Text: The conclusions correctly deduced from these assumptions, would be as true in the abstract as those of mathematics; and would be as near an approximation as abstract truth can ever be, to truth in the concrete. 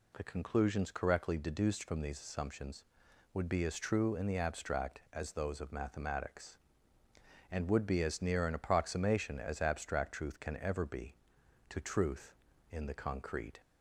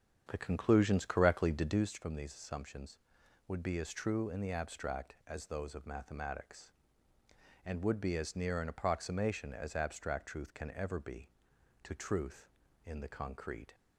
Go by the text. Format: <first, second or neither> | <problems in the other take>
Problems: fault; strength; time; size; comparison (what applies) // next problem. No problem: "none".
first | starts louder than the rest; strong; until 1.8 s; 8 dB